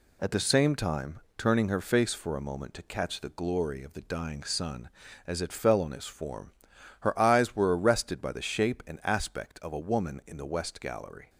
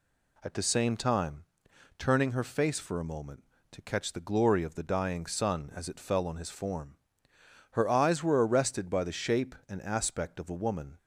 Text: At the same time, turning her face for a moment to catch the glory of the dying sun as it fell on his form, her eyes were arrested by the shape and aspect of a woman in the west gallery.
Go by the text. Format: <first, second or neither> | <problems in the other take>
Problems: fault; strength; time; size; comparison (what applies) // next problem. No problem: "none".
first | stops before "in the west gallery"; at 10.9 s